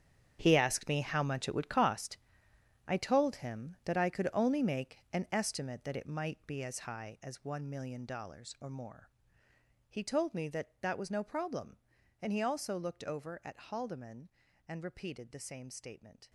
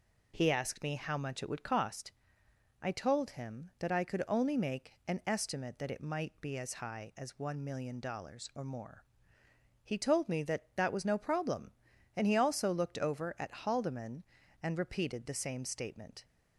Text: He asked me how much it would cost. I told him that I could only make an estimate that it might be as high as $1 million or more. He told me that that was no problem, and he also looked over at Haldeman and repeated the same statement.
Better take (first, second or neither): second